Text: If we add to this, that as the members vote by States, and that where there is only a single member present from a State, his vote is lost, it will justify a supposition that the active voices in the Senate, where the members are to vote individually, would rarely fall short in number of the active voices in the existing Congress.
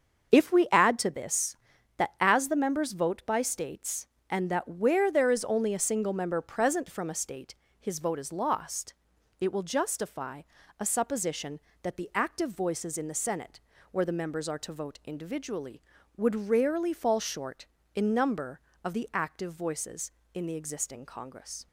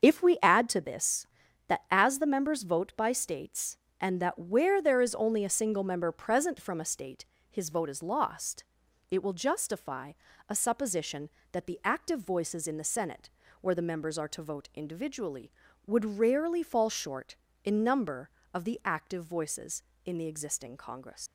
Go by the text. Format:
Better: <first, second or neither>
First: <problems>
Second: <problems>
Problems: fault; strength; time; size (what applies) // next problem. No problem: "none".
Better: first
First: starts louder than the rest; until 1.3 s; 6.5 dB // pauses between "justify" and "a"; at 10.4 s; 0.40 s long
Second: starts louder than the rest; until 1.0 s; 6.5 dB // pauses between "justify" and "a"; at 10.1 s; 0.39 s long // leaves "Congress" unfinished; at 21.2 s; 120 ms